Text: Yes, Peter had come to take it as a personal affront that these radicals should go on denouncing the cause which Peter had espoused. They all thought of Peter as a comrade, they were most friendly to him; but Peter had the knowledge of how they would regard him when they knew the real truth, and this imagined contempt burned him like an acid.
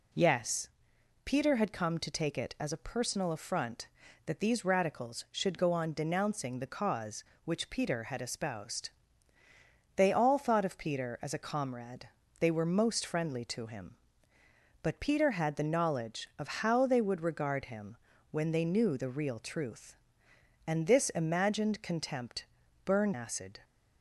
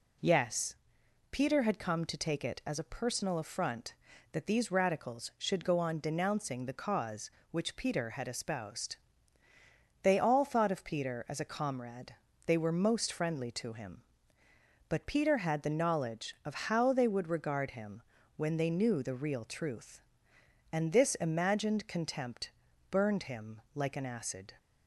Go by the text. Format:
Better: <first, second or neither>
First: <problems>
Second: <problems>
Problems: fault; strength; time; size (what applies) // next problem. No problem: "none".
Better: second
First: pauses between "him" and "when"; slight; at 17.9 s; 0.36 s long // pauses between "contempt" and "burned"; at 22.4 s; 0.38 s long // skips "him like an"; at 23.1 s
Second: pauses between "him" and "when"; slight; at 18.0 s; 0.36 s long // pauses between "contempt" and "burned"; at 22.5 s; 0.38 s long